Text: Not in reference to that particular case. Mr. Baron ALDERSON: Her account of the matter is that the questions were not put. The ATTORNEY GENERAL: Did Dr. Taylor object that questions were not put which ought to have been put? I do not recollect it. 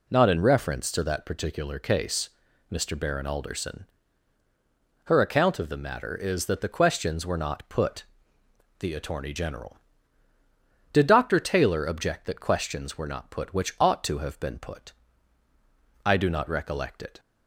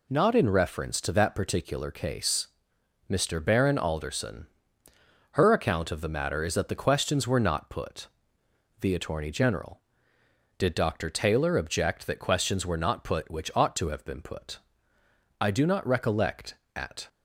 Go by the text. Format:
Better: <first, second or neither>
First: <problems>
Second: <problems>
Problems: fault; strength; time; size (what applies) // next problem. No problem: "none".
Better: first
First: none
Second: says "at" for "it"; at 16.7 s